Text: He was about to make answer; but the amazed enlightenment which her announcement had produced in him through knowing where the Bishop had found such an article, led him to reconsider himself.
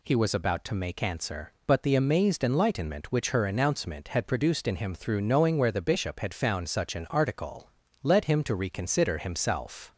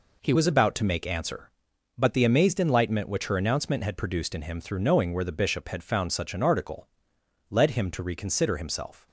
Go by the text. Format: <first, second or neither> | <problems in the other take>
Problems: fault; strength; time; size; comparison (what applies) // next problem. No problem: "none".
first | changes voice at "was"; from 0.3 s on; 8.7 s long